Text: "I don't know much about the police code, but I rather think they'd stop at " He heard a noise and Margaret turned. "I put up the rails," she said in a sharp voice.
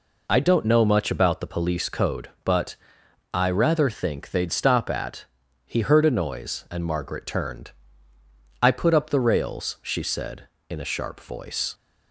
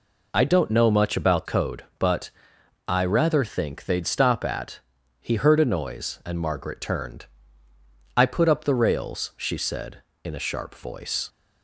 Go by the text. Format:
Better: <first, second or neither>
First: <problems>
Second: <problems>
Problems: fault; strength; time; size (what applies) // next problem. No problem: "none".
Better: first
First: pauses between "but" and "I"; noticeable; at 2.7 s; 0.58 s long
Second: skips "the police"; at 1.4 s // pauses between "but" and "I"; noticeable; at 2.3 s; 0.58 s long